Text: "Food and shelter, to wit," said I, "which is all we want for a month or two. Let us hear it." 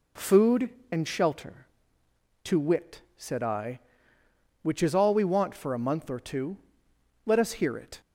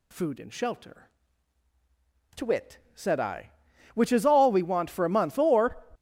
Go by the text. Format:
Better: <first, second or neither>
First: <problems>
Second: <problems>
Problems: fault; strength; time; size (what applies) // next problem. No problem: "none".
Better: first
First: none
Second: stops before "two Let us hear it"; at 5.9 s